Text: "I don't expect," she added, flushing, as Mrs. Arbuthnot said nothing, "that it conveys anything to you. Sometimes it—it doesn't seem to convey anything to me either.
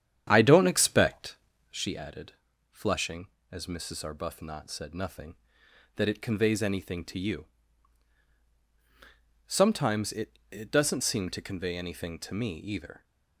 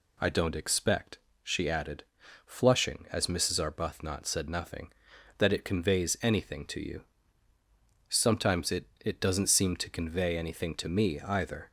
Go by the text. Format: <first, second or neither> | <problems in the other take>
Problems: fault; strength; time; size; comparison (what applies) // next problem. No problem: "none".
second | starts louder than the rest; strong; until 1.8 s; 9.5 dB